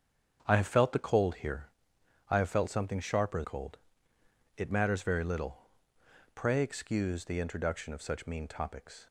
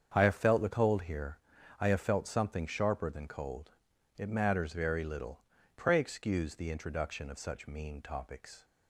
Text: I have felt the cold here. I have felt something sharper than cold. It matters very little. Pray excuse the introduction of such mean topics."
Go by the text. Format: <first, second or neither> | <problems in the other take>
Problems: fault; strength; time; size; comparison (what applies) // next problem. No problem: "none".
second | starts louder than the rest; strong; until 1.4 s; 7.5 dB; strong in the second // skips "than"; at 3.4 s